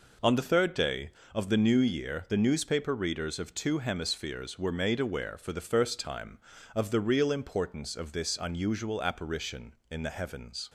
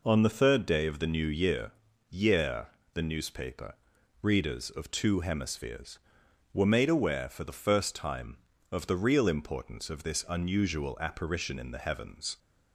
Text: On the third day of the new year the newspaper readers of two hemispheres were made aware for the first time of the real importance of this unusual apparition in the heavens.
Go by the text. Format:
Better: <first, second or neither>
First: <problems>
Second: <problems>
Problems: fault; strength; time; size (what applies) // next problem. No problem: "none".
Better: first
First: none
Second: says "year" twice; at 2.0 s // pauses between "newspaper" and "readers"; noticeable; at 3.7 s; 0.48 s long